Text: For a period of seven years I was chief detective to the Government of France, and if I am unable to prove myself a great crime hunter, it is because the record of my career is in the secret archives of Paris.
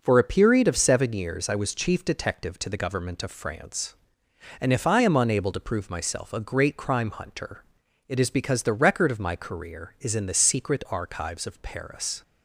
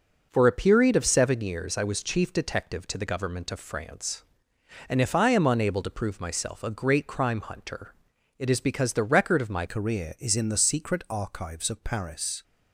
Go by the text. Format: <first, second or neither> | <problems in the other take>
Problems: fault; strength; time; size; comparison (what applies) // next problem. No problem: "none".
first | changes voice at "career"; from 9.6 s on; 2.8 s long